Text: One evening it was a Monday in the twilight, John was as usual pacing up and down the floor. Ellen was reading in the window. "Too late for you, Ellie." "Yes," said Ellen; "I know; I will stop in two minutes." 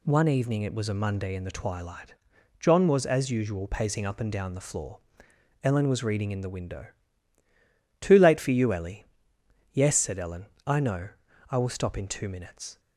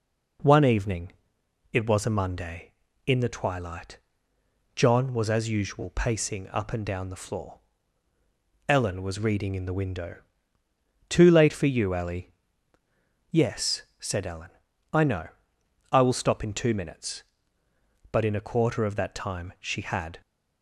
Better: first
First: none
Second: pauses between "evening" and "it"; noticeable; at 1.1 s; 0.58 s long // goes on to say "But in a quarter of that time she had"; strong; from 18.1 s on; 2.1 s long

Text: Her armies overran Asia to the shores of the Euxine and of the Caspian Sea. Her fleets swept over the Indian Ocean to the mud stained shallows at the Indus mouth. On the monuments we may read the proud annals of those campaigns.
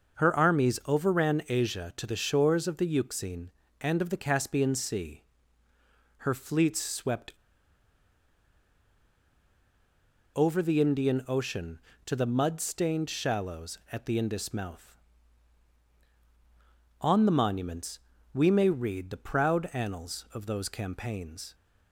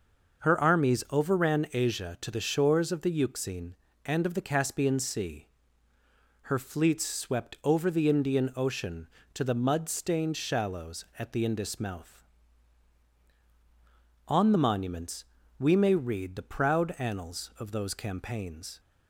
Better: second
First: pauses between "swept" and "over"; strong; at 7.3 s; 3.0 s long // pauses between "monuments" and "we"; slight; at 17.9 s; 0.34 s long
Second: pauses between "monuments" and "we"; slight; at 15.2 s; 0.34 s long

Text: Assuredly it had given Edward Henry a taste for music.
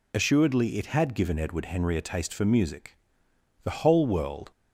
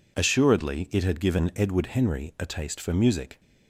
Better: second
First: goes on to say "The whole world"; noticeable; from 3.6 s on; 0.88 s long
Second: none

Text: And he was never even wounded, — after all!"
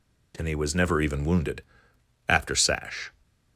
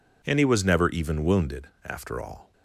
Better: second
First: says "sash" for "all"; at 2.5 s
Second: none

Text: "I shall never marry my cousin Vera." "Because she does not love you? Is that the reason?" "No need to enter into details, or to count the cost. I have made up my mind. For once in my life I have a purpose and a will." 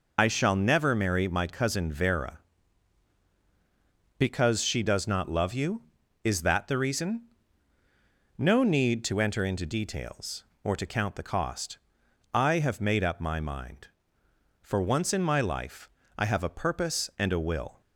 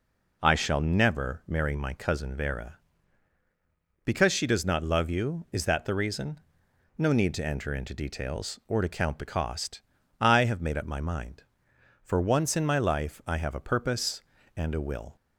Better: second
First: loses the start of "I"; at 0.1 s; 75 ms // pauses between "life" and "I"; slight; at 15.8 s; 0.30 s long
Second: none

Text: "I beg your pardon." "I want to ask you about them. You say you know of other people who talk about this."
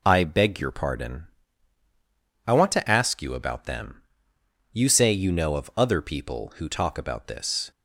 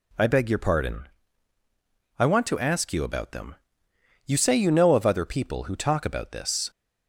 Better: neither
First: none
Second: none

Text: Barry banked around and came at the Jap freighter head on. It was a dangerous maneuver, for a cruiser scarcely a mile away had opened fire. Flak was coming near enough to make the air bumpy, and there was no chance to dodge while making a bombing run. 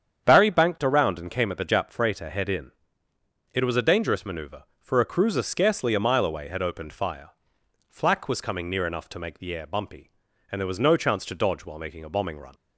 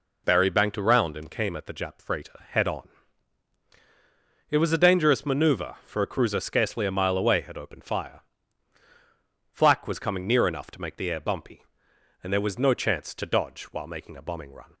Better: second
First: starts louder than the rest; strong; until 1.2 s; 8 dB // says "in" for "on"; at 2.4 s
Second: none

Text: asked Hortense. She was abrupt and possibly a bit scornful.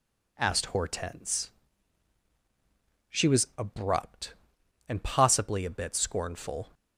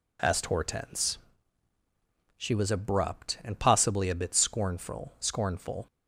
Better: first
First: none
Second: says "scornful" twice; at 5.1 s

